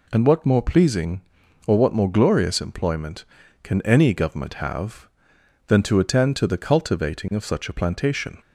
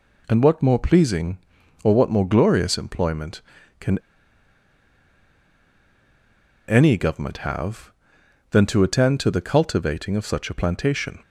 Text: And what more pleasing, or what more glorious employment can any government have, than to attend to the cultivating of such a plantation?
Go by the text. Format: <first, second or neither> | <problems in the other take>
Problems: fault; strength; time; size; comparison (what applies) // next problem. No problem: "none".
first | pauses between "can" and "any"; strong; at 3.9 s; 2.7 s long